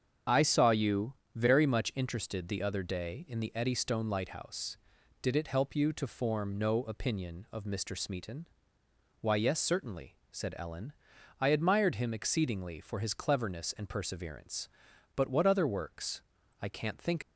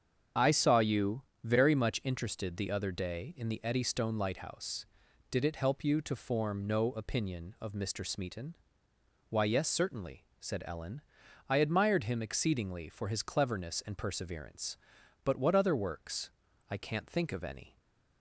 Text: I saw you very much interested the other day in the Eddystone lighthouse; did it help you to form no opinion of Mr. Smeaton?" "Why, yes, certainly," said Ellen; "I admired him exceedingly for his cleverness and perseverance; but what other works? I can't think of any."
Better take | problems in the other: second | starts louder than the rest; strong; until 1.5 s; 7.5 dB; strong in the second // pauses between "you" and "very"; slight; at 1.1 s; 0.20 s long; slight in the second // stops before "of any"; at 17.2 s

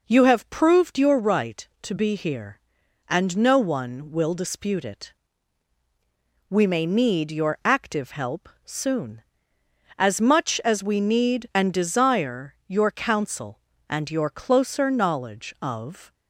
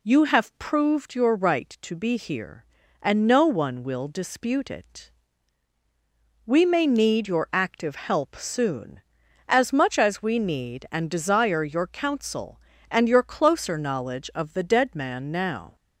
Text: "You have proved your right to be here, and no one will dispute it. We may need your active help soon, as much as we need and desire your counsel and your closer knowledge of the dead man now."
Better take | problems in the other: second | pauses between "help" and "soon"; slight; at 8.4 s; 0.16 s long // stops before "the dead man now"; at 16.1 s

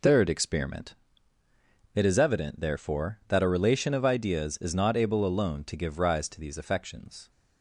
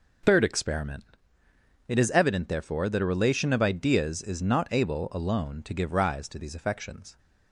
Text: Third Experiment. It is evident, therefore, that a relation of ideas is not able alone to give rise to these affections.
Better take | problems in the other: neither | none

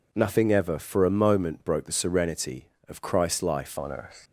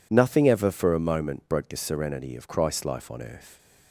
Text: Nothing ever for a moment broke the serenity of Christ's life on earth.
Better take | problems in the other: second | changes voice at "on"; from 3.7 s on; 0.5 s long

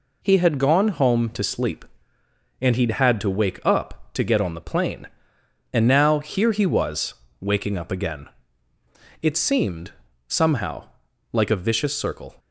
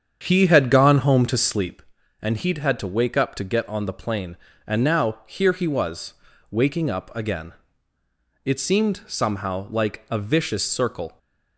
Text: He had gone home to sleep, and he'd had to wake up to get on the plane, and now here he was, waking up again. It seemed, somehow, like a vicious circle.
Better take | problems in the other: first | starts louder than the rest; strong; until 1.8 s; 8 dB

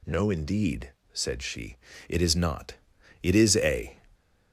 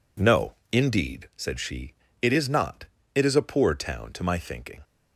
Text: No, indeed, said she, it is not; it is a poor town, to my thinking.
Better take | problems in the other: second | stops before "poor town to my thinking"; at 4.1 s

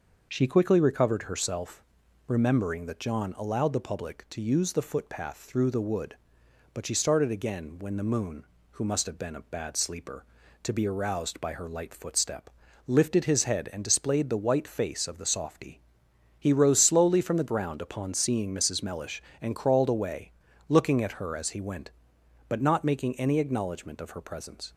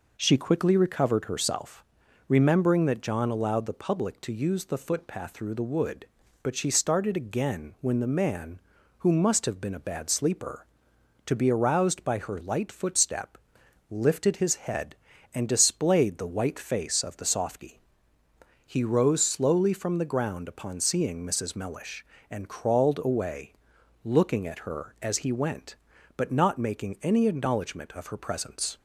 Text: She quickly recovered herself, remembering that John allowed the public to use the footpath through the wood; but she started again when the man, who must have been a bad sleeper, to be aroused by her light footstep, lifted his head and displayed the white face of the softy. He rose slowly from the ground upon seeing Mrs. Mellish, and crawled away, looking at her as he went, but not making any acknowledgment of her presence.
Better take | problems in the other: second | says "moon" for "man"; at 8.0 s

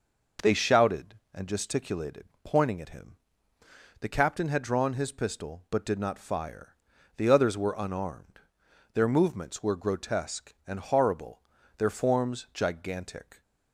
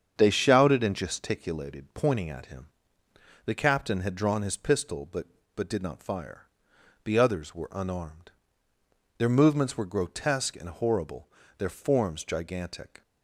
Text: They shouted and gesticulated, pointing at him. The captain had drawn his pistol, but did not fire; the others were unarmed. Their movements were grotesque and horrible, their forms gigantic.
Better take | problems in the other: first | starts louder than the rest; strong; until 1.1 s; 7.5 dB // says "but" twice; at 5.5 s

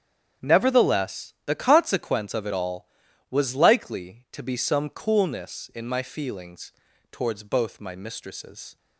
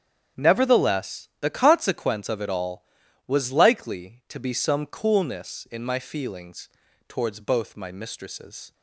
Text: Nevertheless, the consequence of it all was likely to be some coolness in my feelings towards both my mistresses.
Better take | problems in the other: neither | starts louder than the rest; strong; the same in both // pauses between "feelings" and "towards"; the same in both

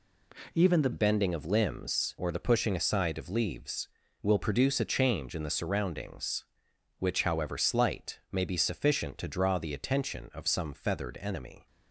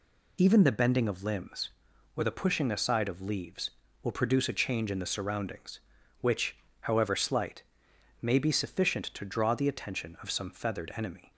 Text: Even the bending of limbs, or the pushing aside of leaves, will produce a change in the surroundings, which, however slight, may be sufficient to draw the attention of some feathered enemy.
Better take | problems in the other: second | changes voice at "bending"; from 0.9 s on; 10.7 s long

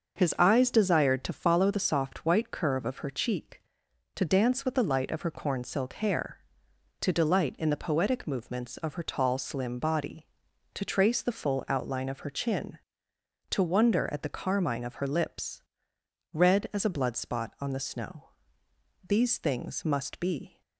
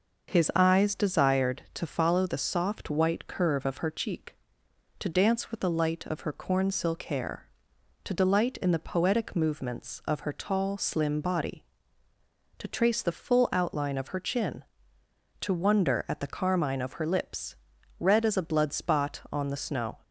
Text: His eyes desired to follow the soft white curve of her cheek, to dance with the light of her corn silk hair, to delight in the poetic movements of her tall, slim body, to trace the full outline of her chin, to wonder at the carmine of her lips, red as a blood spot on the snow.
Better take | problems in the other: second | starts louder than the rest; until 1.2 s; 6.5 dB // goes on to say "These things must be"; from 19.0 s on; 1.5 s long

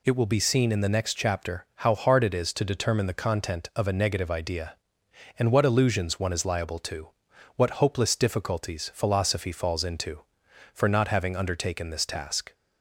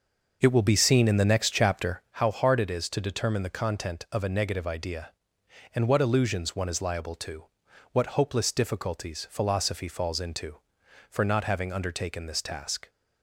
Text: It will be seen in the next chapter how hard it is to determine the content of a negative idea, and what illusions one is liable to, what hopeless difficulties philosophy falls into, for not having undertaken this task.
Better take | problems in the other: first | starts louder than the rest; noticeable; until 2.2 s; 5.5 dB

